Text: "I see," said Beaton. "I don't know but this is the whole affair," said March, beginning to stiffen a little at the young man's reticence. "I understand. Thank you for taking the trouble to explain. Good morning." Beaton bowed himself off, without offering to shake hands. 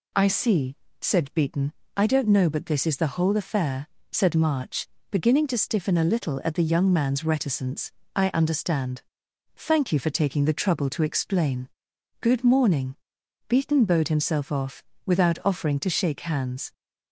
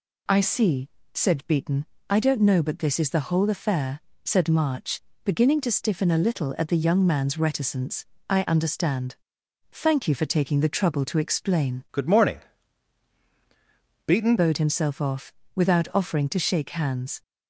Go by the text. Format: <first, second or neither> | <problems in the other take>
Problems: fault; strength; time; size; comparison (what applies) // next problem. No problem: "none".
first | changes voice from "Good" to "Beaton"; from 11.9 to 14.3 s; 2.4 s long